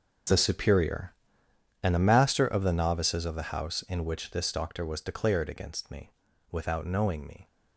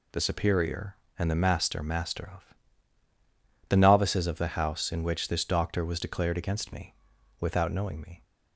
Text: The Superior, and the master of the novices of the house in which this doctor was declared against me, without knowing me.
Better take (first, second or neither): first